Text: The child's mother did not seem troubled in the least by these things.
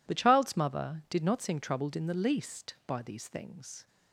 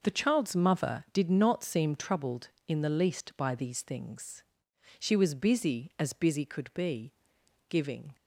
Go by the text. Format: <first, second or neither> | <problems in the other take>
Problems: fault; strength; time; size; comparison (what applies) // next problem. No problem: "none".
first | goes on to say "She was busy as busy could be giving"; strong; from 4.9 s on; 3.1 s long